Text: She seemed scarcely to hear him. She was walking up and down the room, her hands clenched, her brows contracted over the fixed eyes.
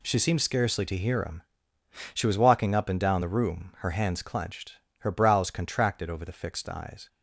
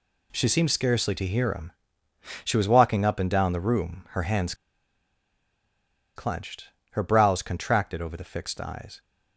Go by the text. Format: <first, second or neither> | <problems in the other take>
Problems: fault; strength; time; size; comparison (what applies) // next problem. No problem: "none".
first | pauses between "hands" and "clenched"; strong; at 4.5 s; 1.6 s long